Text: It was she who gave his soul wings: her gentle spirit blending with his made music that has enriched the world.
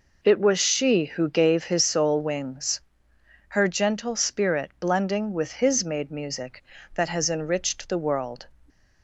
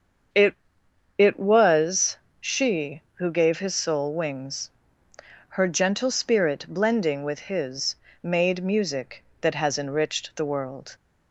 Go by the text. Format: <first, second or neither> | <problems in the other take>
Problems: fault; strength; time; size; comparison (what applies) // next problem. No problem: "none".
first | starts louder than the rest; until 1.9 s; 7 dB // says "It" twice; at 1.1 s // pauses between "was" and "she"; slight; at 2.1 s; 0.24 s long // pauses between "his" and "made"; slight; at 7.9 s; 0.26 s long